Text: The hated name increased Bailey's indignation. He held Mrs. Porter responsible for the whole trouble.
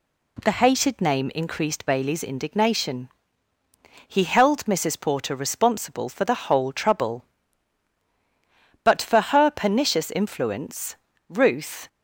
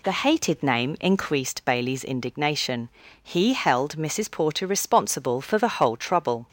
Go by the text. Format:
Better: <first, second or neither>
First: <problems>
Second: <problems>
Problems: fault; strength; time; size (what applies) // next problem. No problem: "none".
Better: second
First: goes on to say "But for her pernicious influence Ruth"; strong; from 8.8 s on; 3.0 s long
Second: none